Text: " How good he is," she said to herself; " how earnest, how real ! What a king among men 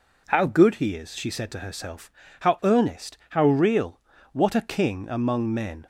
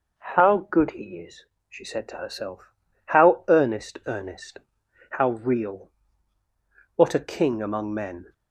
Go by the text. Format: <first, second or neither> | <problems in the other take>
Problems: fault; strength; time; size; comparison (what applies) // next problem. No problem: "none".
first | says "earnest" twice; at 4.0 s